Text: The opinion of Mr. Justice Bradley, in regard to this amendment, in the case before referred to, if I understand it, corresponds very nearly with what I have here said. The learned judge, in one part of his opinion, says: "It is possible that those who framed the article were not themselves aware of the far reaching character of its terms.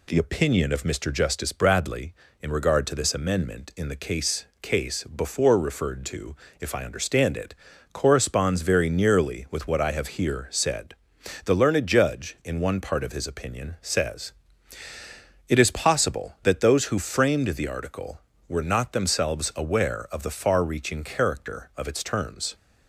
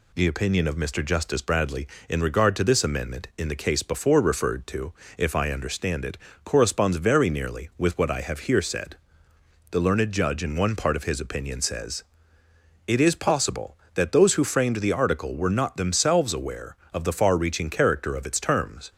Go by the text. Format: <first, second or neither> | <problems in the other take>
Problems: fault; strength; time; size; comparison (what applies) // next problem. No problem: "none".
second | says "case" twice; at 4.6 s